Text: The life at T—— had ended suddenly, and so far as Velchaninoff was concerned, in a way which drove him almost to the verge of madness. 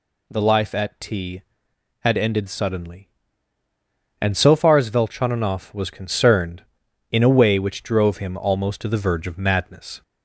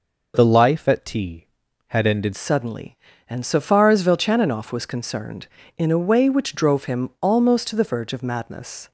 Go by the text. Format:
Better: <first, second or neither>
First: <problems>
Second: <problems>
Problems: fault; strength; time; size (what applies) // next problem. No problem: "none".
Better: first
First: none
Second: changes voice at "suddenly"; from 2.3 s on; 6.6 s long